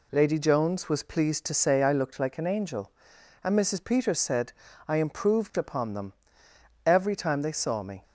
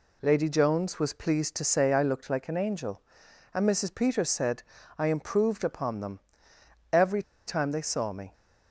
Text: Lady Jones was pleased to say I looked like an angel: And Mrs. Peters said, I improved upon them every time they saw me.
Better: first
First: pauses between "them" and "every"; noticeable; at 6.1 s; 0.72 s long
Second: pauses between "them" and "every"; noticeable; at 6.1 s; 0.72 s long // pauses between "every" and "time"; slight; at 7.2 s; 0.25 s long

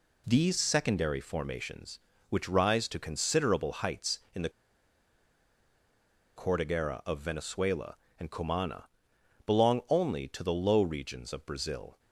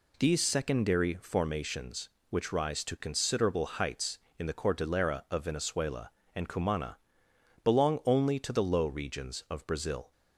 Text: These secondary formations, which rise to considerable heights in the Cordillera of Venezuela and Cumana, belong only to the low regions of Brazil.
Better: second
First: pauses between "the" and "Cordillera"; strong; at 4.4 s; 1.8 s long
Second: none

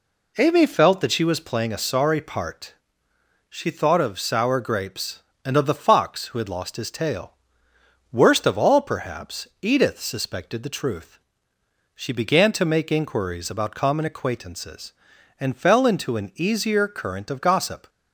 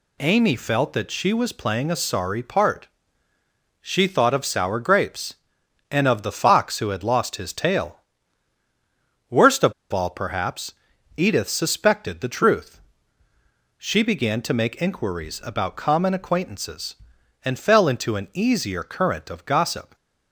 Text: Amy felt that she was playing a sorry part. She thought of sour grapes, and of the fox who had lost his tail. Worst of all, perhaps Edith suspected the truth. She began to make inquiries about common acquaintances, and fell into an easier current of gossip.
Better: first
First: pauses between "perhaps" and "Edith"; slight; at 9.4 s; 0.16 s long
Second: pauses between "of" and "all"; slight; at 9.7 s; 0.19 s long // pauses between "perhaps" and "Edith"; at 10.7 s; 0.44 s long

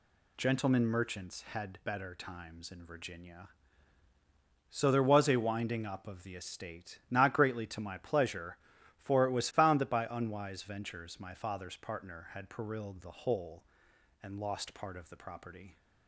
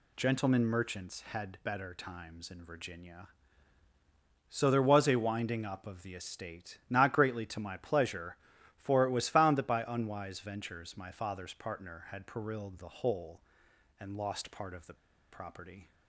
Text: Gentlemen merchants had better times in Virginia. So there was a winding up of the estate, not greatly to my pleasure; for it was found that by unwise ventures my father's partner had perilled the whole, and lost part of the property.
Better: first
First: none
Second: pauses between "the" and "property"; at 14.9 s; 0.38 s long

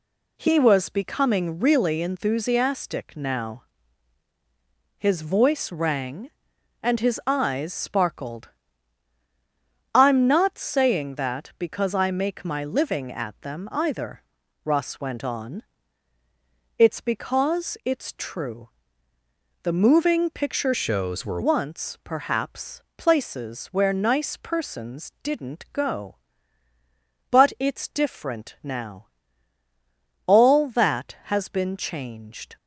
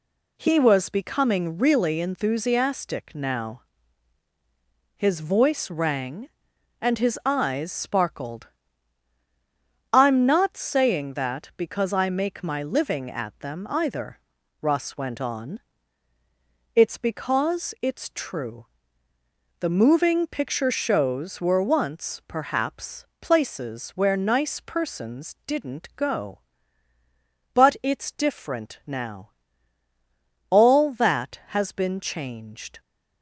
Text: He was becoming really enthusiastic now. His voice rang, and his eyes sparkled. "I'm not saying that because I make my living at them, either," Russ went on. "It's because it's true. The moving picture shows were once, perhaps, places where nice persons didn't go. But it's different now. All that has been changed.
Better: second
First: changes voice from "shows" to "were"; from 20.7 to 21.3 s; 0.6 s long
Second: none

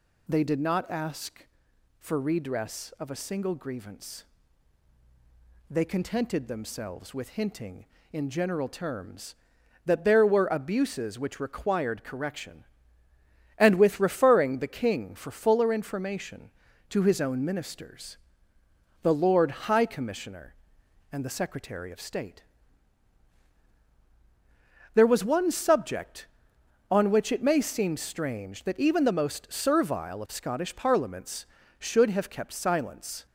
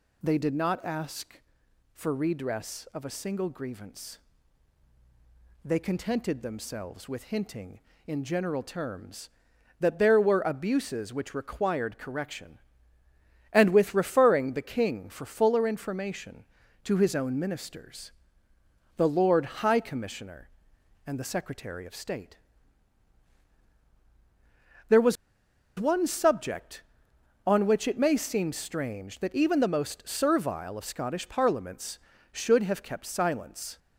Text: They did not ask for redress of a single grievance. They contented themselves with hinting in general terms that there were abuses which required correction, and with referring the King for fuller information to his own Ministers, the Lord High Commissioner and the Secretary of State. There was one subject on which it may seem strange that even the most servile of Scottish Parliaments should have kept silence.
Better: first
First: none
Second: pauses between "was" and "one"; noticeable; at 25.1 s; 0.62 s long

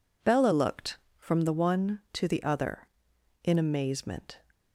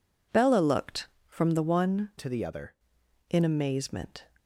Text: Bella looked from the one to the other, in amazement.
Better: first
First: none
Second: changes voice from "to" to "other"; from 2.1 to 2.7 s; 0.6 s long

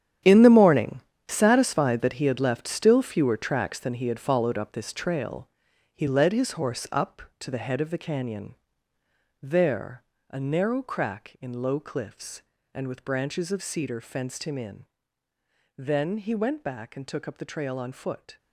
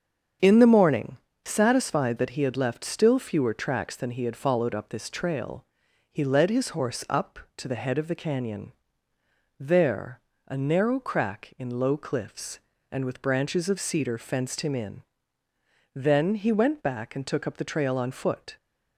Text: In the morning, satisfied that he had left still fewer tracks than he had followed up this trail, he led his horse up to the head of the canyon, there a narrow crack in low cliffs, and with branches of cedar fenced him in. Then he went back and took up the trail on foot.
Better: second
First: gets quieter; strong; throughout; 13 dB // starts louder than the rest; strong; until 1.5 s; 10 dB // pauses between "there" and "a"; slight; at 10.0 s; 0.28 s long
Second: starts louder than the rest; strong; until 1.6 s; 7.5 dB // pauses between "there" and "a"; slight; at 10.1 s; 0.28 s long

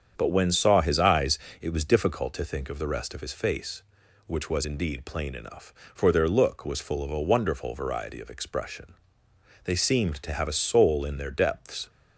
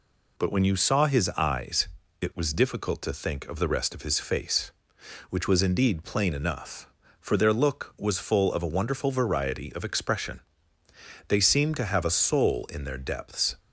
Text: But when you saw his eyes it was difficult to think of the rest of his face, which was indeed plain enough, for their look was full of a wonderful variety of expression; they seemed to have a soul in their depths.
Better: second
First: starts louder than the rest; strong; until 1.1 s; 7.5 dB // skips "you"; at 0.5 s // pauses between "eyes" and "it"; slight; at 1.3 s; 0.22 s long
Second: pauses between "eyes" and "it"; slight; at 1.8 s; 0.32 s long

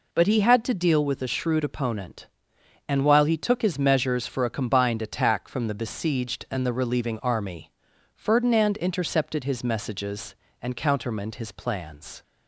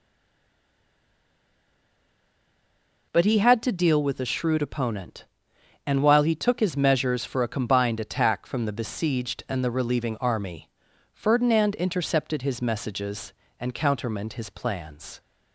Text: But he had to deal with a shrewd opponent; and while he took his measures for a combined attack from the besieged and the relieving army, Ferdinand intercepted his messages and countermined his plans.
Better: first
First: none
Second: stays silent before the first word; strong; until 3.1 s; 3.1 s long

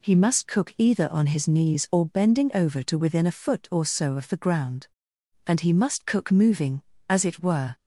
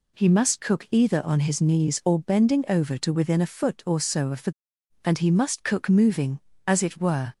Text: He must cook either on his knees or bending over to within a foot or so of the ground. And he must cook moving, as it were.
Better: first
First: none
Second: skips "ground"; at 4.7 s

